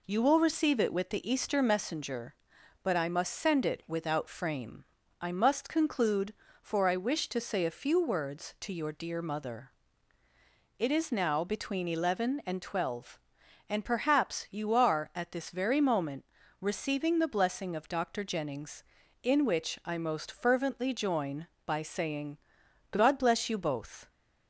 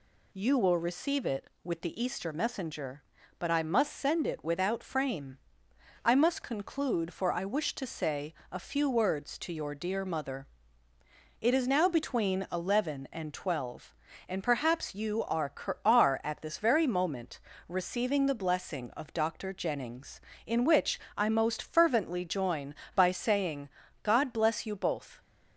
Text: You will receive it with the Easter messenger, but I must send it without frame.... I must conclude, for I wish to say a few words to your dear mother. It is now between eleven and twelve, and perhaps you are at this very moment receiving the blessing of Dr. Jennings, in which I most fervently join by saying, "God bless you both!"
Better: first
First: pauses between "moment" and "receiving"; slight; at 16.2 s; 0.34 s long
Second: pauses between "say" and "a"; slight; at 8.3 s; 0.16 s long // says "are" twice; at 15.8 s // pauses between "moment" and "receiving"; slight; at 17.3 s; 0.30 s long // pauses between "which" and "I"; slight; at 20.9 s; 0.20 s long

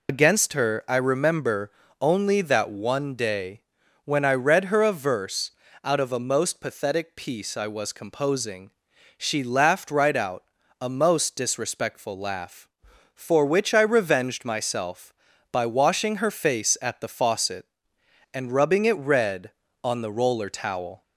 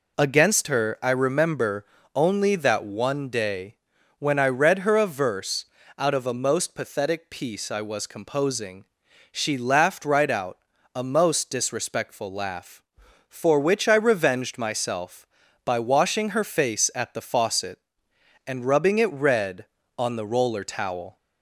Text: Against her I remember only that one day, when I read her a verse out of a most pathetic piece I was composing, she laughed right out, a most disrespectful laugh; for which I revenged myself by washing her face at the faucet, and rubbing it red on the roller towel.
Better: second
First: loses the start of "Against"; at 0.0 s; 80 ms // pauses between "remember" and "only"; slight; at 1.7 s; 0.28 s long // pauses between "verse" and "out"; slight; at 5.5 s; 0.32 s long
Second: pauses between "remember" and "only"; slight; at 1.8 s; 0.28 s long // pauses between "verse" and "out"; slight; at 5.6 s; 0.32 s long

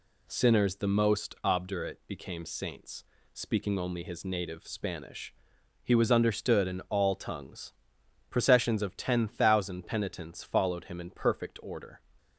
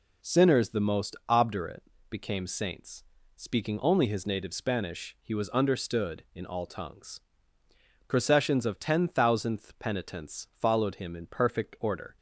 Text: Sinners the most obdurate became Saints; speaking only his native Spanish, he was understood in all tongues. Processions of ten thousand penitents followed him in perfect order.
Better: first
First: none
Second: pauses between "obdurate" and "became"; slight; at 1.8 s; 0.30 s long // says "thousandth" for "thousand"; at 9.0 s

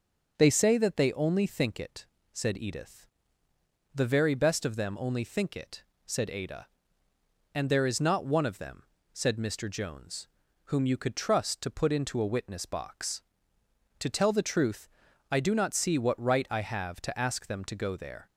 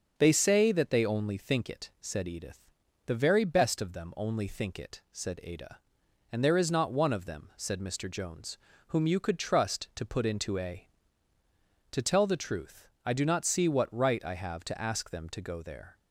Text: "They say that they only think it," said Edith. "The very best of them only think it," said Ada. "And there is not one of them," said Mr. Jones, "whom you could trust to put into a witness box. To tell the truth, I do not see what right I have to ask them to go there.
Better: first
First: starts louder than the rest; until 1.3 s; 6.5 dB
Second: starts louder than the rest; until 1.1 s; 6.5 dB // skips "witness box"; at 11.3 s

